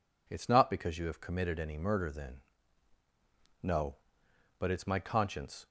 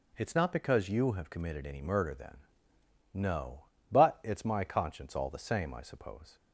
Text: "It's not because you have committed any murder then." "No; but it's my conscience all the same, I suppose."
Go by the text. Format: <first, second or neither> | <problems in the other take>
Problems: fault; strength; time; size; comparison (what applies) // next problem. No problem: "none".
second | stops before "all the same I suppose"; at 5.6 s